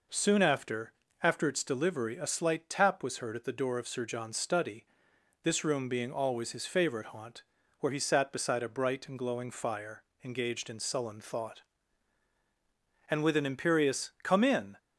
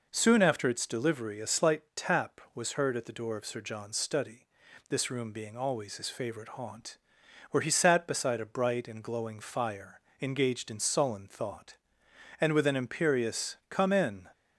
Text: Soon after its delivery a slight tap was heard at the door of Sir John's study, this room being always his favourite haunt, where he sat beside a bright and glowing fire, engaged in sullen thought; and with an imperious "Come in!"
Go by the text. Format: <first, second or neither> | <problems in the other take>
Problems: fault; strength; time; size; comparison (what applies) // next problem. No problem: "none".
second | says "after" twice; at 1.2 s